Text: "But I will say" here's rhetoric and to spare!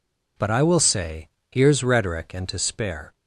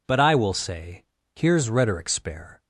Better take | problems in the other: first | pauses between "say" and "here's"; slight; at 1.0 s; 0.32 s long; slight in the first // skips "and to"; at 2.0 s

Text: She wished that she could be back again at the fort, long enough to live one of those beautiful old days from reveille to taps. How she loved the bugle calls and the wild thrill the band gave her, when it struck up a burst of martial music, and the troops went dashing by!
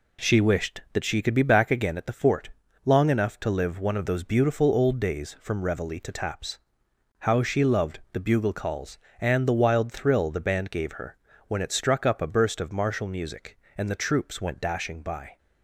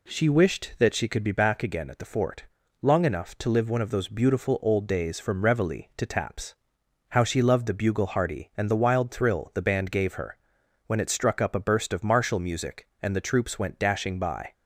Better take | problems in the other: first | says "hearty" for "calls"; at 8.0 s

